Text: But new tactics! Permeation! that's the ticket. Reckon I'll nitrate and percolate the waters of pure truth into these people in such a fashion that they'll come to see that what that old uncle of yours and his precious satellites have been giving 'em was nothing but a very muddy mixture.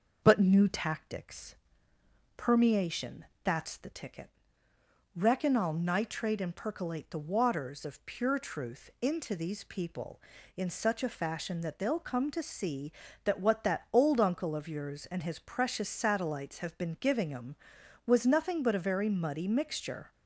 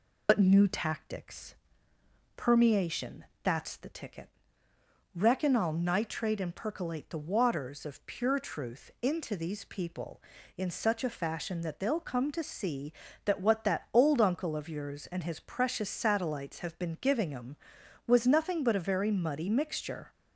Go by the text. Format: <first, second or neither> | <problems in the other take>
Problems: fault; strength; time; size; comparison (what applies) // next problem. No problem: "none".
first | loses the start of "But"; at 0.2 s; 65 ms